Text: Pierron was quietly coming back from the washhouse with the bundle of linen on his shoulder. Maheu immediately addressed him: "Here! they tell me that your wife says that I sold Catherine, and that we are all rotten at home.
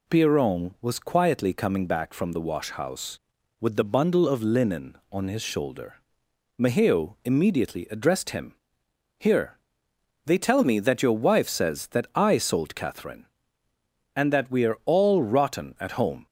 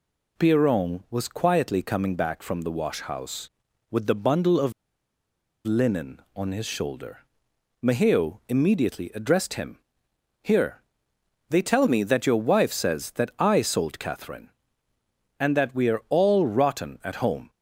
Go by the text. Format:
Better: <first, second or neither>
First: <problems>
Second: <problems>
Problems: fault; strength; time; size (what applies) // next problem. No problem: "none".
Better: first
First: none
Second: pauses between "of" and "linen"; noticeable; at 4.7 s; 0.93 s long